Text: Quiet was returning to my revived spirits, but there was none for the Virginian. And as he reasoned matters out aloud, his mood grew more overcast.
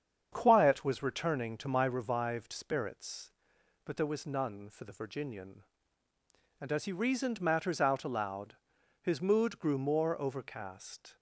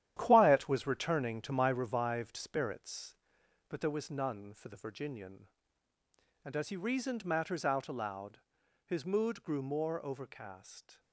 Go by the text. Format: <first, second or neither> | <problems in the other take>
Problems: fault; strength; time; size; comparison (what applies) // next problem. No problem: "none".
first | gets quieter; strong; throughout; 8.5 dB // starts louder than the rest; strong; until 1.1 s; 11 dB; strong in the first